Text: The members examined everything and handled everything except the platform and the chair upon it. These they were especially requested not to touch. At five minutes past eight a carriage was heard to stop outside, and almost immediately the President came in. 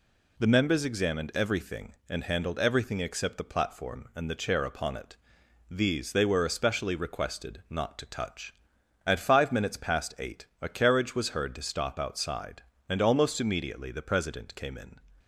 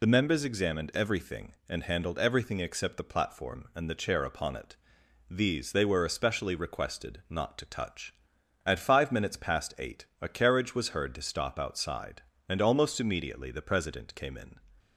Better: first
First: pauses between "eight" and "a"; slight; at 10.4 s; 0.16 s long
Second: loses the start of "The"; at 0.0 s; 35 ms // pauses between "eight" and "a"; slight; at 10.0 s; 0.16 s long

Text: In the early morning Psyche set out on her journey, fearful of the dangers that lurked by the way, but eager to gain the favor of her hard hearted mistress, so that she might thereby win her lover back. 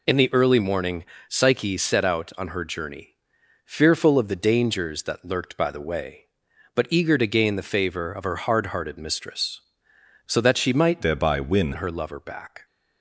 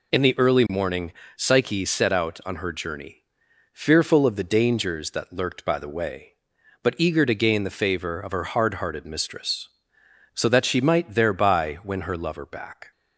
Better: second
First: pauses between "morning" and "Psyche"; slight; at 1.0 s; 0.24 s long // changes voice from "thereby" to "win"; from 11.0 to 11.7 s; 0.7 s long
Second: pauses between "morning" and "Psyche"; slight; at 1.1 s; 0.24 s long

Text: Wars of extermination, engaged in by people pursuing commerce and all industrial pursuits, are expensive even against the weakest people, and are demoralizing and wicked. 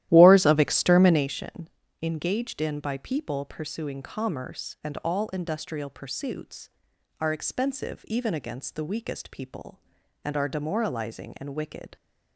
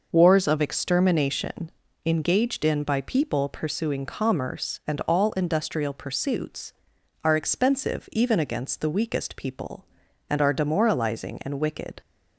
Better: second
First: starts louder than the rest; strong; until 1.3 s; 13.5 dB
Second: none

